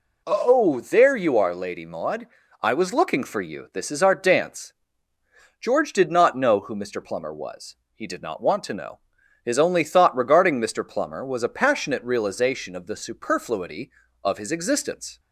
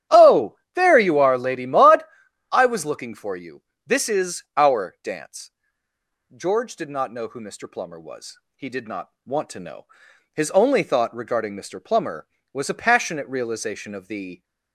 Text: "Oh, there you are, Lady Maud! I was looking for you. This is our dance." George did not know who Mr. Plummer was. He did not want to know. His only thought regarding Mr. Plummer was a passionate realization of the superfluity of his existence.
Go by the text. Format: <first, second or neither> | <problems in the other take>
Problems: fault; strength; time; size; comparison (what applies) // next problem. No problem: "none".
first | starts louder than the rest; strong; until 1.3 s; 11 dB // pauses between "not" and "want"; slight; at 9.0 s; 0.16 s long // stops before "superfluity of his existence"; at 14.4 s